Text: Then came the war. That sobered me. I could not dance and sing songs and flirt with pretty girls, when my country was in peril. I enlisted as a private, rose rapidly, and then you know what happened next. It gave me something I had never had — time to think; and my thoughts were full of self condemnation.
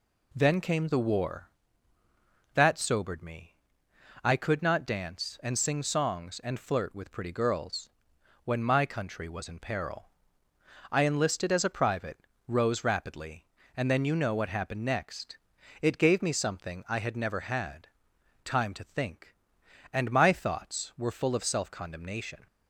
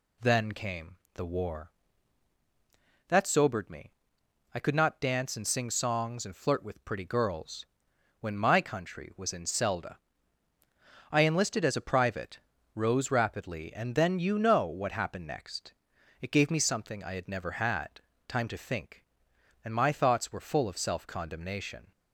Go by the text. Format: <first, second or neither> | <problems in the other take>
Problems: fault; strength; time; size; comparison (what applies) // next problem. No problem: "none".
first | pauses between "came" and "the"; slight; at 0.9 s; 0.18 s long // says "selda" for "peril"; at 9.4 s